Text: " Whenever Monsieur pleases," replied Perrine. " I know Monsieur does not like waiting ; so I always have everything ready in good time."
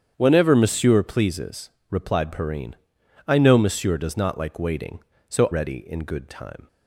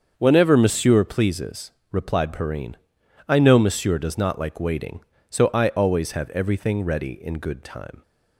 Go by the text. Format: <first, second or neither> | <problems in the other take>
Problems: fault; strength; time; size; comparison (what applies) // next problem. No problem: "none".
second | starts louder than the rest; strong; until 1.1 s; 8 dB; also in the second // skips "I always have everything"; at 5.5 s